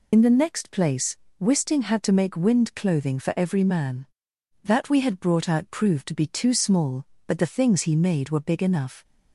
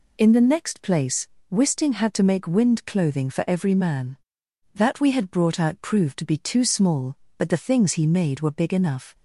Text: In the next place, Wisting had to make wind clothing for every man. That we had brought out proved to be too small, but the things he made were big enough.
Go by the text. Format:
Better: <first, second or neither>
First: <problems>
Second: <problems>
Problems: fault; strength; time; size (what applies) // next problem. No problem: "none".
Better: second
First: loses the start of "In"; at 0.1 s; 50 ms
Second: none